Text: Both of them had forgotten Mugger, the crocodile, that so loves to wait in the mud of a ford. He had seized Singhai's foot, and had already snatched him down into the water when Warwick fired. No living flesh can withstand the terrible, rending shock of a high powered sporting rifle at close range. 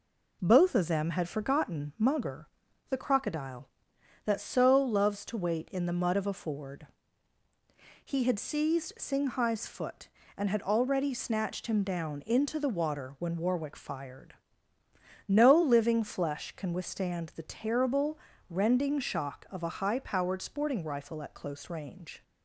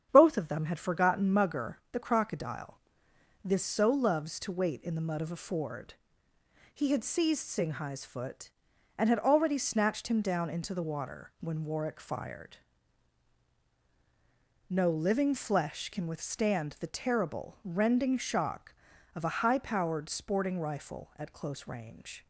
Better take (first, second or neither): first